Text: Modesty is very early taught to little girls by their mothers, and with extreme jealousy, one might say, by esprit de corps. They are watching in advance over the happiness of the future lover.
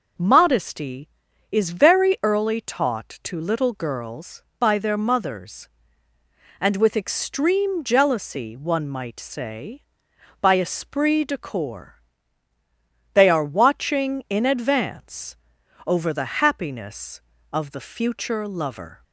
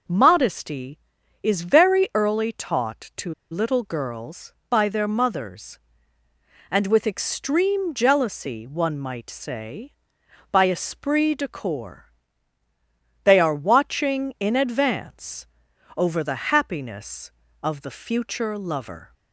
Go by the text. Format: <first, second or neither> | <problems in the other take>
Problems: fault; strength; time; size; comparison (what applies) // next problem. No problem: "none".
first | pauses between "to" and "little"; slight; at 3.3 s; 0.18 s long // pauses between "advance" and "over"; noticeable; at 15.4 s; 0.50 s long; noticeable in the first